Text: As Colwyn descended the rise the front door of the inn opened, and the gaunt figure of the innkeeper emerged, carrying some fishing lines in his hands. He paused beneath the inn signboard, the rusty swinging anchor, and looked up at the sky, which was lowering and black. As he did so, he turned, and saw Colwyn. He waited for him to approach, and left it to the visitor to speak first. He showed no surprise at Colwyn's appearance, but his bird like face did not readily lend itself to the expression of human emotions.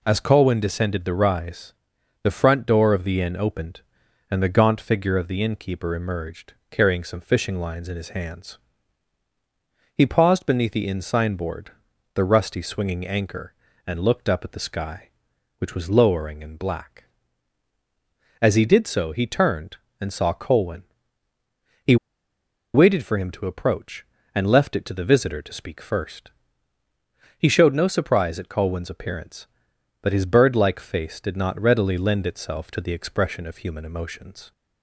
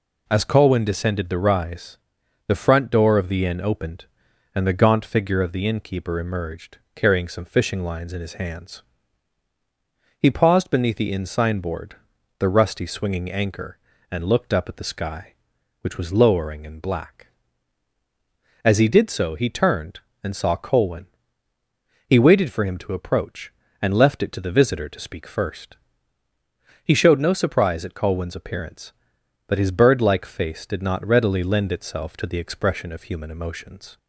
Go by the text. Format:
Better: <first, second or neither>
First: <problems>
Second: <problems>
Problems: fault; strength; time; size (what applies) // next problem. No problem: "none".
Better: second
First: pauses between "rise" and "the"; noticeable; at 1.7 s; 0.50 s long // pauses between "He" and "waited"; noticeable; at 21.9 s; 0.78 s long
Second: pauses between "rise" and "the"; noticeable; at 1.9 s; 0.50 s long